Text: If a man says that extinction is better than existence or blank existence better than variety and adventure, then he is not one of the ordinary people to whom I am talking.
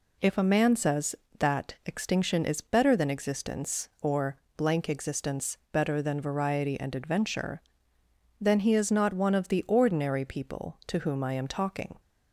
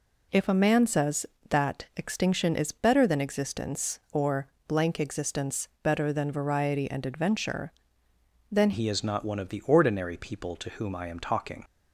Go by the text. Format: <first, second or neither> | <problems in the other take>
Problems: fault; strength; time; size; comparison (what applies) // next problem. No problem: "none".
first | pauses between "or" and "blank"; slight; at 4.4 s; 0.20 s long; slight in the first // changes voice at "he"; from 8.7 s on; 2.9 s long